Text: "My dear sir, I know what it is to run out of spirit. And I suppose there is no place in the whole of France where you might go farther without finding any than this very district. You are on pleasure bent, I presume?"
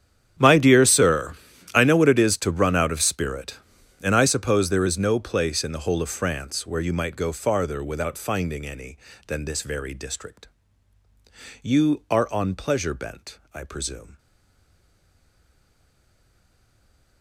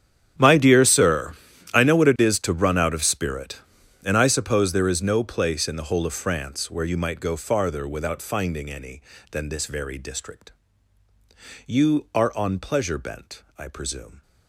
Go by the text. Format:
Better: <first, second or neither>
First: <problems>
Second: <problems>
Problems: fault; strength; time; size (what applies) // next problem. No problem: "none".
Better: second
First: starts louder than the rest; strong; until 1.8 s; 10.5 dB // stays silent after the last word; strong; from 14.1 s on; 3.1 s long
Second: starts louder than the rest; strong; until 1.7 s; 10.5 dB